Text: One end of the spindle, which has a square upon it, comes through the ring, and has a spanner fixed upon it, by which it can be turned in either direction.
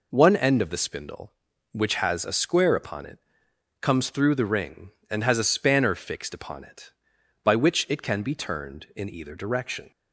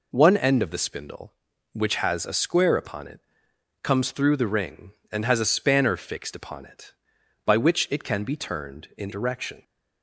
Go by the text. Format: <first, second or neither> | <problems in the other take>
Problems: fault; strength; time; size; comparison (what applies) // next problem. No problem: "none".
first | skips "either"; at 9.1 s